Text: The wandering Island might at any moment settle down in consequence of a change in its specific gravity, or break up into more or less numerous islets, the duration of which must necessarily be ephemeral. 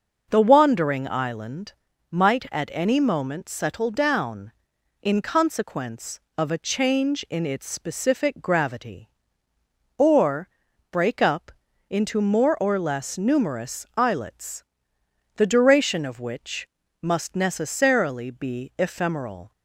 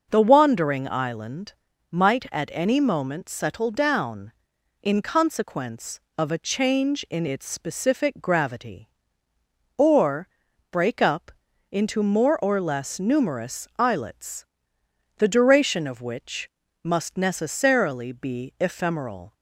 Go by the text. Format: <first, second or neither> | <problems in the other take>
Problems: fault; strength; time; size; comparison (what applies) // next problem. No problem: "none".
neither | pauses between "Island" and "might"; the same in both // pauses between "or" and "break"; the same in both // pauses between "up" and "into"; the same in both // pauses between "which" and "must"; slight; the same in both